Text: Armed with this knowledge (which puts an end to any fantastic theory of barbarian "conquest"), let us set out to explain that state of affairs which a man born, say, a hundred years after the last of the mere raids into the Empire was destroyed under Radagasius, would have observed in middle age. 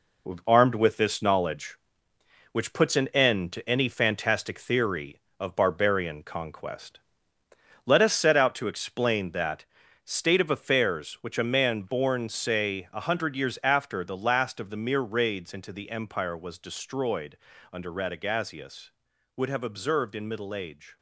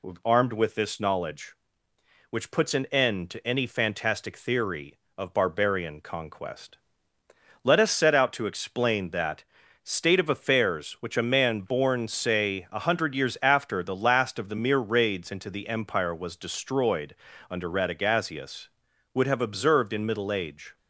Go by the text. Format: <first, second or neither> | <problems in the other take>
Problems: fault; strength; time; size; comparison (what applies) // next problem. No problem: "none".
second | gets quieter; throughout; 6 dB // pauses between "that" and "state"; at 9.6 s; 0.38 s long; also in the second // pauses between "destroyed" and "under"; slight; at 17.3 s; 0.34 s long; slight in the second